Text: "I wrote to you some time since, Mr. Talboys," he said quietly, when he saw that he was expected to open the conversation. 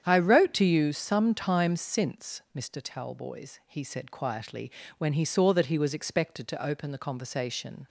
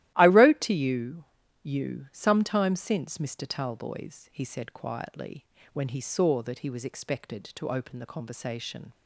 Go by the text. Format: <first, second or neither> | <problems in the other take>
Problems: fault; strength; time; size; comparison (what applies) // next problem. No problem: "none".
first | starts louder than the rest; strong; until 1.1 s; 14.5 dB; strong in the first // says "you" twice; at 1.6 s